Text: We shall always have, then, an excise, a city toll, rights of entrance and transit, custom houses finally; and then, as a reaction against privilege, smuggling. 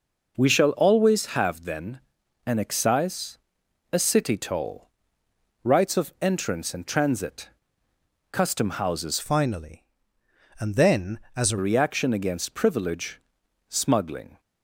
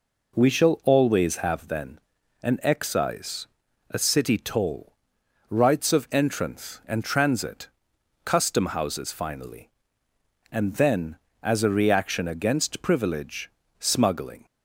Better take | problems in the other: second | changes voice from "finally" to "a"; from 9.1 to 11.5 s; 2.4 s long

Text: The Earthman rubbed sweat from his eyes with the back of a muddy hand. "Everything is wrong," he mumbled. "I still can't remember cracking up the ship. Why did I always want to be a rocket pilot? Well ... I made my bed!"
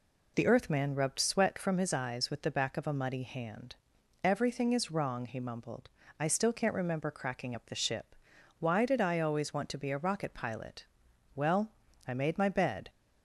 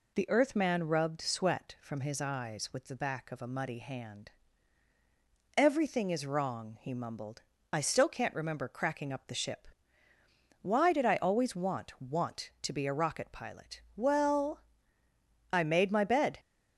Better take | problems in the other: first | says "want" twice; at 12.0 s

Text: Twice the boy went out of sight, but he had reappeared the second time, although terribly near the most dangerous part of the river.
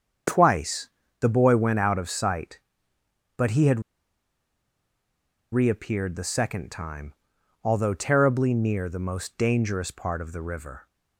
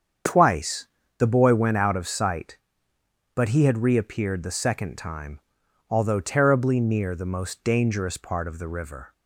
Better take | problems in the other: second | starts louder than the rest; strong; until 1.5 s; 7.5 dB; strong in the second // pauses between "Twice" and "the"; slight; at 0.9 s; 0.30 s long; slight in the second // pauses between "had" and "reappeared"; strong; at 3.8 s; 1.7 s long

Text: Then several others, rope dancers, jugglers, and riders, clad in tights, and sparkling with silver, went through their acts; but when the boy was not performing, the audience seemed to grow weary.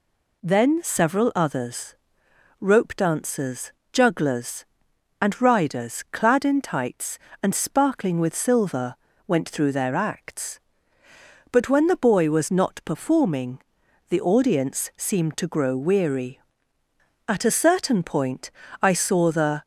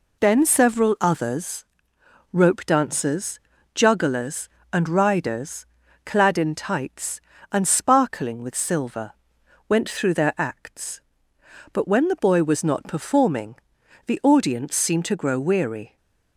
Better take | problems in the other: second | goes on to say "At a certain point I saw the"; strong; from 17.2 s on; 2.3 s long

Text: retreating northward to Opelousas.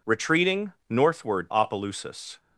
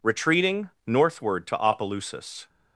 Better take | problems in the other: second | pauses between "retreating" and "northward"; slight; at 0.7 s; 0.16 s long; slight in the second // skips "to"; at 1.5 s

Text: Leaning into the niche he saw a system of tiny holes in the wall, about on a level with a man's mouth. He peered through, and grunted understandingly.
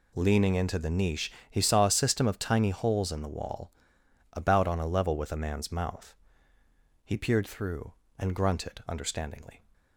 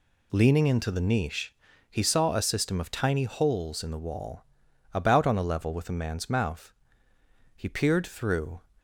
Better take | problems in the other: first | pauses between "niche" and "he"; slight; at 1.5 s; 0.36 s long; slight in the first // stops before "and grunted understandingly"; at 8.7 s

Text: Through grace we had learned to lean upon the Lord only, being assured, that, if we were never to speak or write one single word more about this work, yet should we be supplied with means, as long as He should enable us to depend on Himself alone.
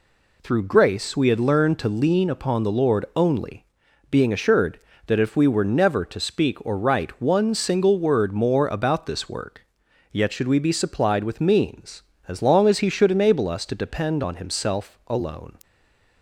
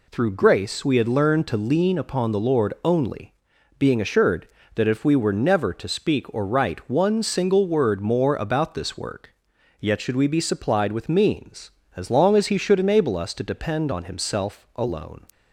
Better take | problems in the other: second | stays silent after the last word; slight; from 15.6 s on; 0.6 s long

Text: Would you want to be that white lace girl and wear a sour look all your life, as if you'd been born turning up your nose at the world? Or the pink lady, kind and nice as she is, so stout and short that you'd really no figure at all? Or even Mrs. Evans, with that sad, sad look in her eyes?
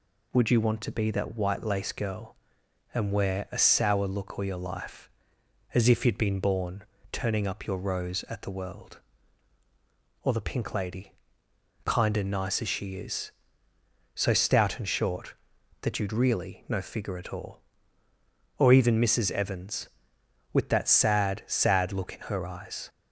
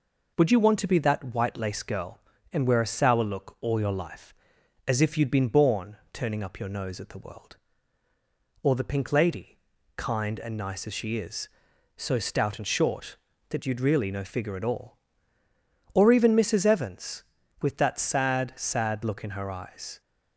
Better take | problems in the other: second | pauses between "born" and "turning"; slight; at 6.8 s; 0.28 s long; slight in the second // says "rose" for "nose"; at 7.7 s

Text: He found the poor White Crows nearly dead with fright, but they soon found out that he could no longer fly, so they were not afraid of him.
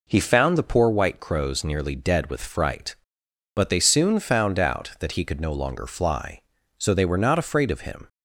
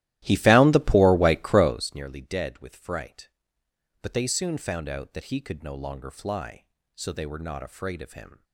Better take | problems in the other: first | starts louder than the rest; strong; until 1.9 s; 15 dB

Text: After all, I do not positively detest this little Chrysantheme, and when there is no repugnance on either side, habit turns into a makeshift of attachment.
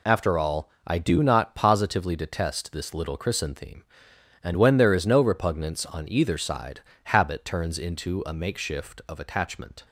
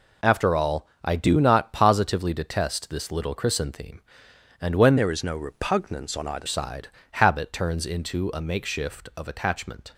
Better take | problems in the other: first | changes voice from "there" to "either"; from 4.9 to 6.4 s; 1.5 s long

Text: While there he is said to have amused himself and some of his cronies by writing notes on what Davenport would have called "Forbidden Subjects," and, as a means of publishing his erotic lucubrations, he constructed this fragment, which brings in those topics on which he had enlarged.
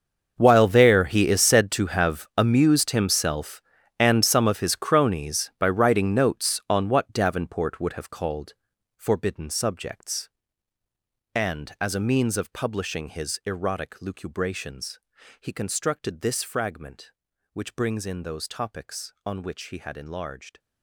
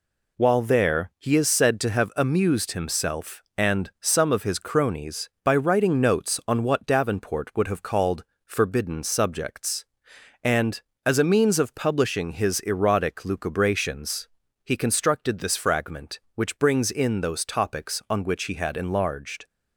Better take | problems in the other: second | gets quieter; strong; throughout; 18 dB // pauses between "called" and "Forbidden"; at 8.5 s; 0.44 s long; slight in the second

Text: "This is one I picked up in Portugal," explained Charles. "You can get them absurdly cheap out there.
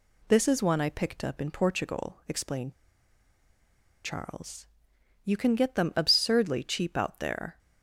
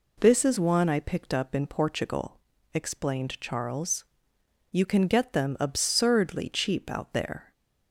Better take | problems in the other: second | pauses between "explained" and "Charles"; strong; at 2.7 s; 1.3 s long

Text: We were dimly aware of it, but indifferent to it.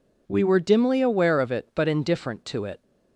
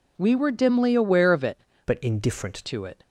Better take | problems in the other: first | changes voice from "but" to "indifferent"; from 1.8 to 2.5 s; 0.7 s long

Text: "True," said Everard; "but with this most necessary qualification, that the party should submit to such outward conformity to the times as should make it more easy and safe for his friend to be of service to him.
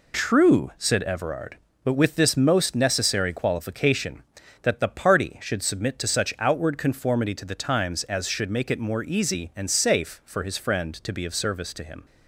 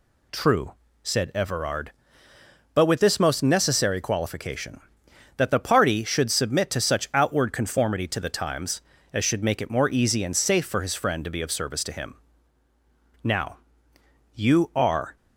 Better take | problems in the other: first | goes on to say "Now you are"; strong; from 13.2 s on; 1.9 s long

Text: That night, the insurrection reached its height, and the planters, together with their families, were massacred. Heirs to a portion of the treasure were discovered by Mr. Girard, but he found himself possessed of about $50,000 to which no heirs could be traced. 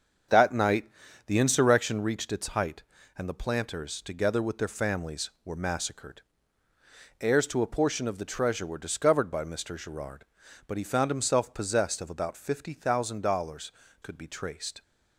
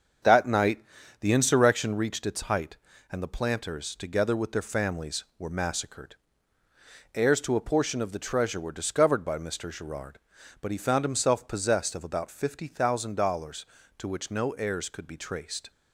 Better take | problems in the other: second | starts louder than the rest; until 1.6 s; 7 dB; also in the second // skips "to which no heirs"; at 13.8 s

